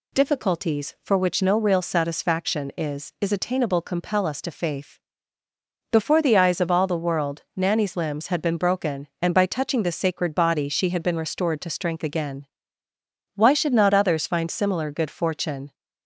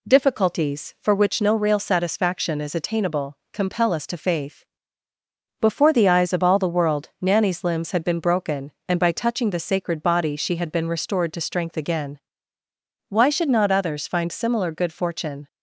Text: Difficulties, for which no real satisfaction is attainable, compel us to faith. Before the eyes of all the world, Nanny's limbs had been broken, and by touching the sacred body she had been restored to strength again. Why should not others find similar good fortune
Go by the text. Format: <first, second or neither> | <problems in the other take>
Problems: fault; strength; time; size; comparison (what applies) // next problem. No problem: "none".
second | says "is" twice; at 3.1 s